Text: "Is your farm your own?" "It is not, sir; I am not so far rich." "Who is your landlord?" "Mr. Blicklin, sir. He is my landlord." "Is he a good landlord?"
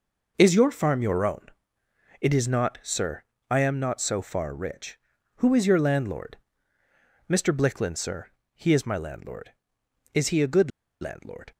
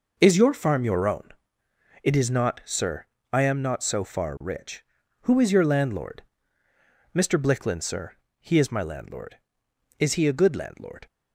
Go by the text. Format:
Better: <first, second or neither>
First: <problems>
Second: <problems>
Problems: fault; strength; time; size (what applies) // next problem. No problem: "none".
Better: second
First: pauses between "good" and "landlord"; slight; at 10.7 s; 0.31 s long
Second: none